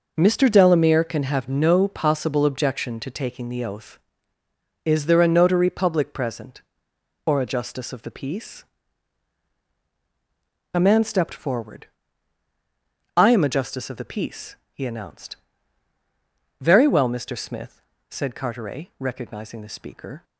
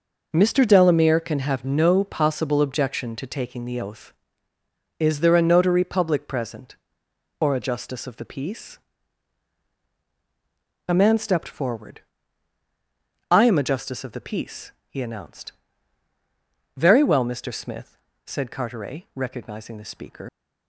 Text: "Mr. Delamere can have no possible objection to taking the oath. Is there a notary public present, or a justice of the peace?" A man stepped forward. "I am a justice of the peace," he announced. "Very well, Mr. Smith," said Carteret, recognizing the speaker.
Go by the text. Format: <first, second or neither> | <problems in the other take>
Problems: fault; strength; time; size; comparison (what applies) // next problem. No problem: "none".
first | leaves "speaker" unfinished; at 20.2 s; 110 ms